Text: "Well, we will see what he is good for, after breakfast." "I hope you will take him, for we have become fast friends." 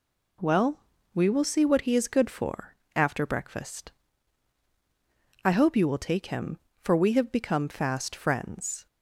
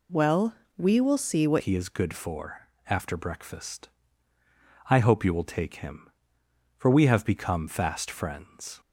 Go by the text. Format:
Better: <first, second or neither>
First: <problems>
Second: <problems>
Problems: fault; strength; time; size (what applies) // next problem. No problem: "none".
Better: first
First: none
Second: changes voice at "he"; from 1.5 s on; 7.2 s long